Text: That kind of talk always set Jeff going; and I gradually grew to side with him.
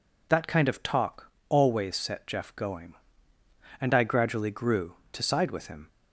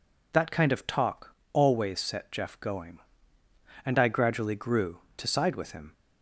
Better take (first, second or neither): neither